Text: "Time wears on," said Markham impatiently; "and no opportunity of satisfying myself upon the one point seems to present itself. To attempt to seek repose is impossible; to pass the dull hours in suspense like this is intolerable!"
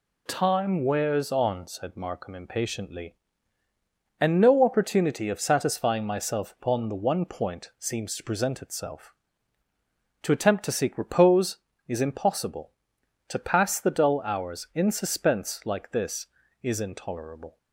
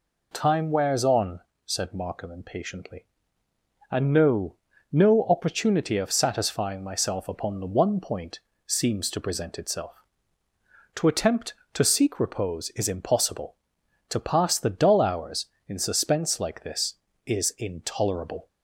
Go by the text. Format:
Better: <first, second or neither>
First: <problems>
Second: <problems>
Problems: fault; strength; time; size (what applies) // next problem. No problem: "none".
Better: first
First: none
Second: says "no" twice; at 4.8 s // pauses between "point" and "seems"; slight; at 8.3 s; 0.26 s long